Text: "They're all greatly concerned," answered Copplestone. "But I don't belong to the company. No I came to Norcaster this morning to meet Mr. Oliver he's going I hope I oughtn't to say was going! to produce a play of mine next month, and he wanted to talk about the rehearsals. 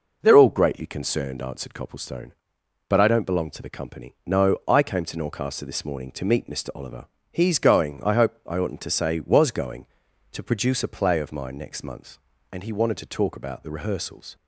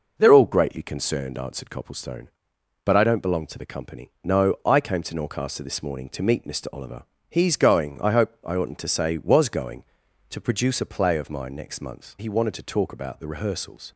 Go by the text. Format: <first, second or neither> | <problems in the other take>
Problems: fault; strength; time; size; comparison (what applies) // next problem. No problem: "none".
first | pauses between "Oliver" and "he's"; slight; at 7.0 s; 0.26 s long; slight in the first // skips "and"; at 12.1 s